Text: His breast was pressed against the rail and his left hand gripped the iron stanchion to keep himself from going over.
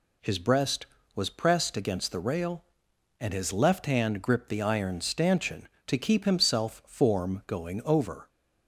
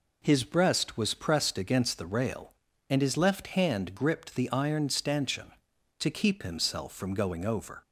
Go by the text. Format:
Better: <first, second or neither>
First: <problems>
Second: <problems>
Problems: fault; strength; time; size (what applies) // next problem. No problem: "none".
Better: second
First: says "form" for "from"; at 6.8 s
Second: none